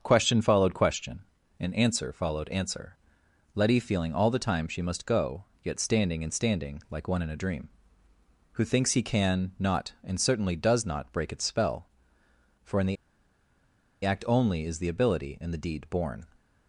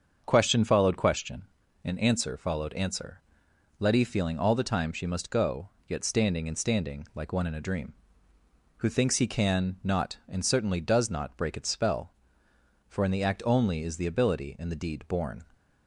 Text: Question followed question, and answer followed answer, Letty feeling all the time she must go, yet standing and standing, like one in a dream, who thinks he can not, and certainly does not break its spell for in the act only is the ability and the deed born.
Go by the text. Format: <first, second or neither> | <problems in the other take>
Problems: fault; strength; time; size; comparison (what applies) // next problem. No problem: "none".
second | starts louder than the rest; until 1.0 s; 7 dB; also in the second // pauses between "the" and "act"; at 12.9 s; 1.0 s long